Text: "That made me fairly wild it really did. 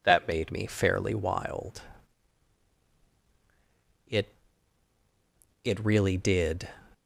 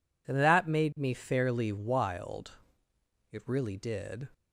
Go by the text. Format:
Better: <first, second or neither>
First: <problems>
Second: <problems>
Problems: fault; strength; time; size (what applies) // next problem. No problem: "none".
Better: second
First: pauses between "wild" and "it"; strong; at 1.8 s; 2.2 s long // says "it" twice; at 5.6 s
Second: pauses between "wild" and "it"; noticeable; at 2.5 s; 0.80 s long